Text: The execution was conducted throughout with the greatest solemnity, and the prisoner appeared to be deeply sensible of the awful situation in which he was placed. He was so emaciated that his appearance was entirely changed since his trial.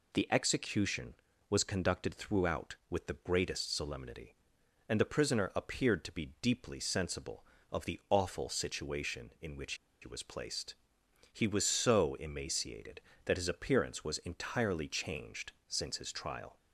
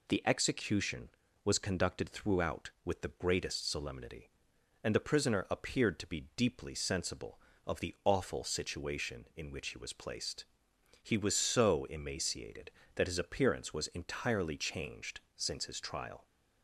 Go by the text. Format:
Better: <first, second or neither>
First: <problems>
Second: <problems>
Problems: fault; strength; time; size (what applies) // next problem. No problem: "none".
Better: second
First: pauses between "which" and "he"; slight; at 9.7 s; 0.27 s long // pauses between "changed" and "since"; slight; at 15.5 s; 0.16 s long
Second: pauses between "changed" and "since"; slight; at 15.2 s; 0.16 s long